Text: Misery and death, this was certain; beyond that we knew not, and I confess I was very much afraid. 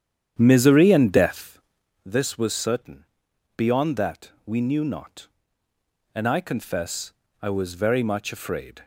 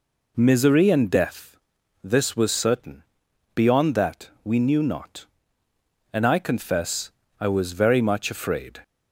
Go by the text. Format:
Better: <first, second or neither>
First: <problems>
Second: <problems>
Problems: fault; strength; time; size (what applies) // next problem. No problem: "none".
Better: second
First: starts louder than the rest; strong; until 2.0 s; 9 dB // pauses between "that" and "we"; slight; at 4.3 s; 0.16 s long // pauses between "confess" and "I"; slight; at 7.1 s; 0.30 s long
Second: pauses between "that" and "we"; slight; at 4.2 s; 0.16 s long // pauses between "confess" and "I"; slight; at 7.1 s; 0.30 s long